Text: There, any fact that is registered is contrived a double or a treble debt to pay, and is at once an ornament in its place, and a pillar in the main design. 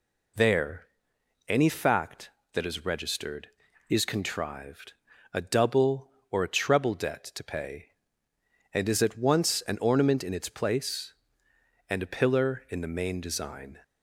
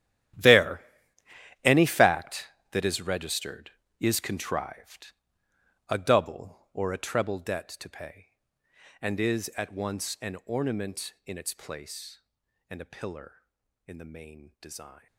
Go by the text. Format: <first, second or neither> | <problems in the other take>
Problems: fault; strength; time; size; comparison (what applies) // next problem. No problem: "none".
first | gets quieter; strong; throughout; 15.5 dB // pauses between "contrived" and "a"; noticeable; at 5.1 s; 0.76 s long; also in the first